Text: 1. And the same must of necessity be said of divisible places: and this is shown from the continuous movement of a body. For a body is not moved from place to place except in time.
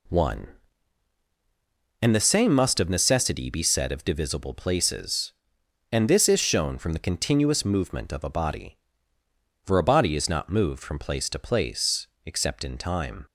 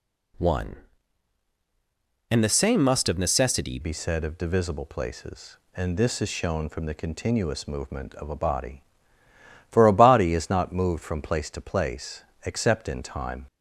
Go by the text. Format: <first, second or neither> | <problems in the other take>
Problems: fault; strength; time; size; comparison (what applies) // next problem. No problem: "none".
first | changes voice at "be"; from 3.8 s on; 9.6 s long // pauses between "place" and "except"; slight; at 12.2 s; 0.22 s long; slight in the first